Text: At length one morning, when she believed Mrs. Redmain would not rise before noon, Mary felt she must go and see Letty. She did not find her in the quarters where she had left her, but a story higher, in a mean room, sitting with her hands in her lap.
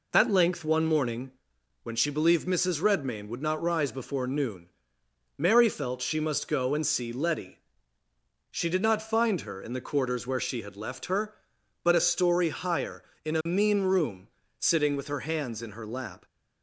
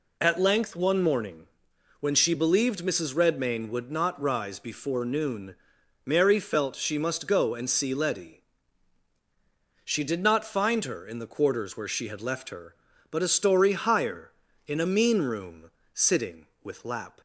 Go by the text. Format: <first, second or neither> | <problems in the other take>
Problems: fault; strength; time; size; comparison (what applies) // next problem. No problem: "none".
first | skips "her hands in her"; at 16.8 s